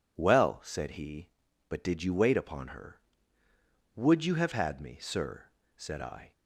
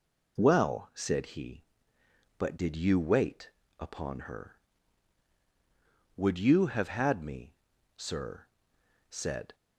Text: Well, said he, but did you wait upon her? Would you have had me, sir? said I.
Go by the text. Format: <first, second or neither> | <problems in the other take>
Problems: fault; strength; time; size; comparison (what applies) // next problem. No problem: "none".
first | pauses between "wait" and "upon"; slight; at 3.5 s; 0.28 s long // stops before "I"; at 9.5 s